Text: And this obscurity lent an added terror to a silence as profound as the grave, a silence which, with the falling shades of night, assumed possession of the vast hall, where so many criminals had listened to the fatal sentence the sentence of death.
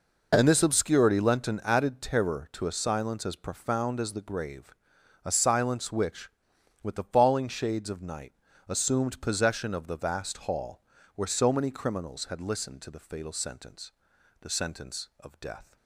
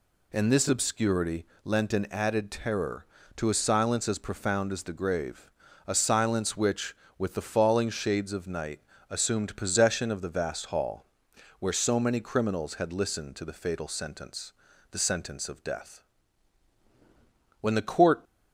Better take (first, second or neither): first